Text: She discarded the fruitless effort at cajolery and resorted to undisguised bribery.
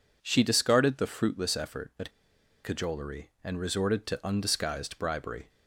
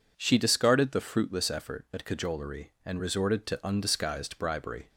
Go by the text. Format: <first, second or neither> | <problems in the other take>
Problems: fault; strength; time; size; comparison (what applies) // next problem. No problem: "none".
second | pauses between "at" and "cajolery"; noticeable; at 2.0 s; 0.54 s long